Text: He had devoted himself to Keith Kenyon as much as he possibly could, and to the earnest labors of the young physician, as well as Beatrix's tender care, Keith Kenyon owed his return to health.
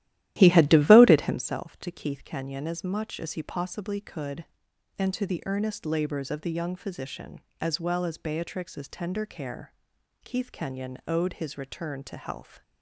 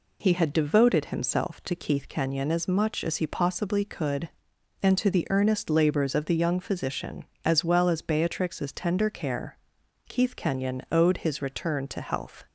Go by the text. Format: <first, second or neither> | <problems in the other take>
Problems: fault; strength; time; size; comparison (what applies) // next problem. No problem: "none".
second | starts louder than the rest; strong; until 1.4 s; 14 dB